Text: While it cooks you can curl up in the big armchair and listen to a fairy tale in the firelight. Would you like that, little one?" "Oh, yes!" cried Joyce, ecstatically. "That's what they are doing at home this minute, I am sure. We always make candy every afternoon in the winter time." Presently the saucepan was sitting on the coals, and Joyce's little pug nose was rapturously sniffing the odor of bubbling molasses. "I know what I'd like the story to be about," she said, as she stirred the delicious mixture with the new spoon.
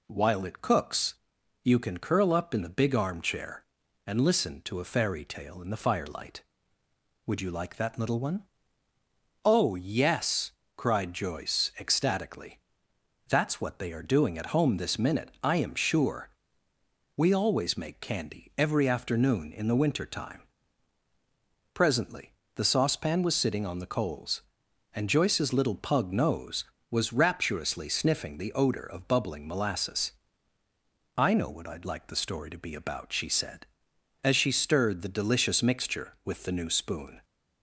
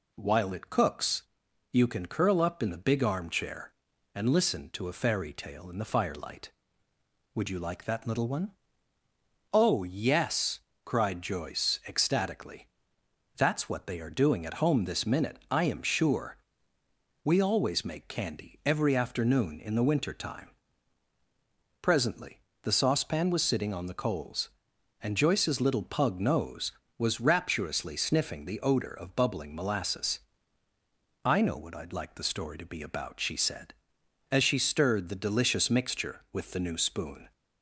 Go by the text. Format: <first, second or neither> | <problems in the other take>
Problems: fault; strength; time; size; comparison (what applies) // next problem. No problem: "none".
neither | pauses between "cooks" and "you"; noticeable; the same in both // pauses between "Presently" and "the"; slight; the same in both